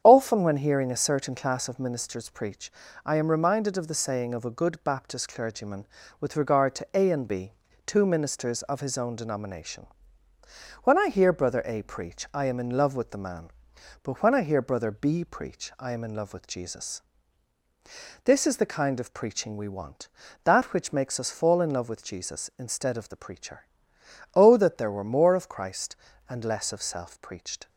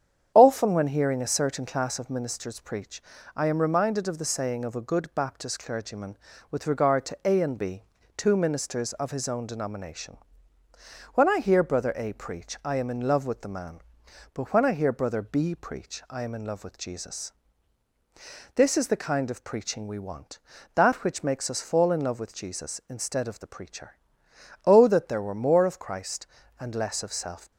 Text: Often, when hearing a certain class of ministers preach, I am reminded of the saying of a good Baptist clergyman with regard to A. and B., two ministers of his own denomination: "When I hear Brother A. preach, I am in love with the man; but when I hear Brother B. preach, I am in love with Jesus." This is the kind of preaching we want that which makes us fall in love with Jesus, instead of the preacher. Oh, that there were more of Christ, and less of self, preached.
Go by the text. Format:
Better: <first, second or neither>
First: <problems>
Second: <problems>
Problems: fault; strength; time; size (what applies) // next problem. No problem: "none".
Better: first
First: starts louder than the rest; strong; until 1.0 s; 8.5 dB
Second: starts louder than the rest; strong; until 1.3 s; 8.5 dB // stops before "preached"; at 27.5 s